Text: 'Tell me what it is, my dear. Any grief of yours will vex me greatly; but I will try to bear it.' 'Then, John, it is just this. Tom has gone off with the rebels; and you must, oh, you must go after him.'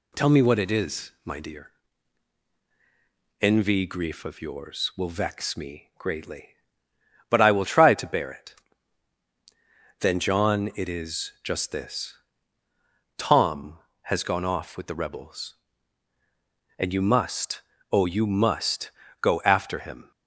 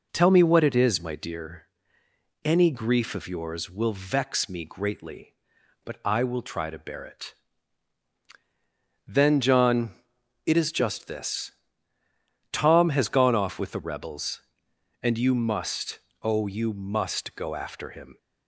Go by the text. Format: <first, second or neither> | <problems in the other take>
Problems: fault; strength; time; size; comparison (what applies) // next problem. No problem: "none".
second | says "Envy" for "Any"; at 3.4 s // pauses between "must" and "go"; slight; at 18.9 s; 0.30 s long